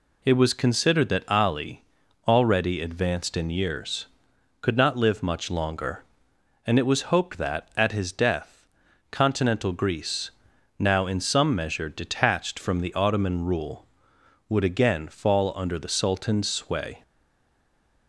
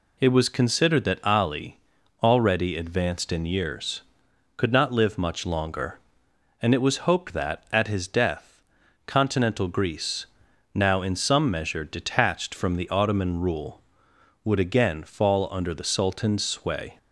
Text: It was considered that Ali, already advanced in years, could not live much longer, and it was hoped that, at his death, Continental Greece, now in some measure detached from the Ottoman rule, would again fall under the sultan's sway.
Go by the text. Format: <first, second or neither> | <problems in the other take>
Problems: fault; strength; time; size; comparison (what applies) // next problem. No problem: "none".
second | stays silent after the last word; from 17.0 s on; 1.0 s long